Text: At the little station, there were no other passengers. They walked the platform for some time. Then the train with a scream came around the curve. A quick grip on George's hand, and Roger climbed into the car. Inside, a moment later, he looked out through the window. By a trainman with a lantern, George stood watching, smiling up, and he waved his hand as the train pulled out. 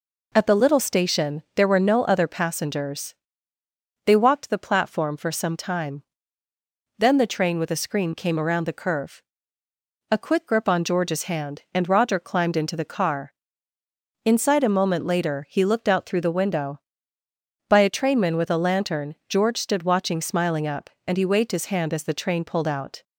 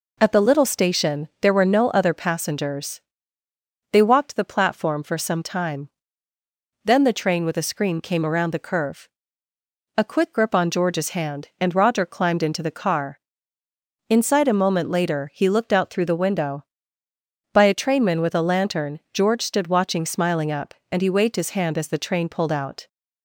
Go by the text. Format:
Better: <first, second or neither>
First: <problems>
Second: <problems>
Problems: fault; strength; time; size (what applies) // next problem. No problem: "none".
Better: neither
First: none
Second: none